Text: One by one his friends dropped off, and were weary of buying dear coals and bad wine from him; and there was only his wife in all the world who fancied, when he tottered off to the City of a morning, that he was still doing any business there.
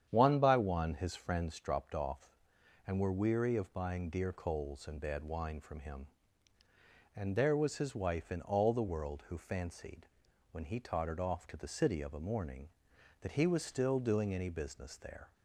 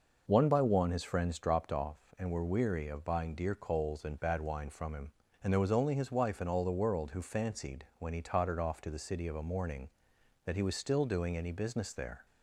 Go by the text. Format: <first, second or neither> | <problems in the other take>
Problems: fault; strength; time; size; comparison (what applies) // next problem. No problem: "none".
second | starts louder than the rest; strong; until 1.1 s; 9 dB // skips "only"; at 7.7 s